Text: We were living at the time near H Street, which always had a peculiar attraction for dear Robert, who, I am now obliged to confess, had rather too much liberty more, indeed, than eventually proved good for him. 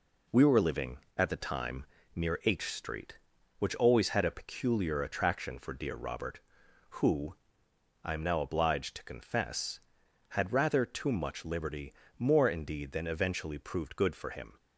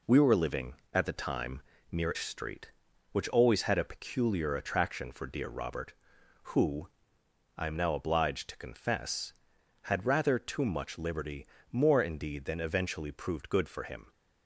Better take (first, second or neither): first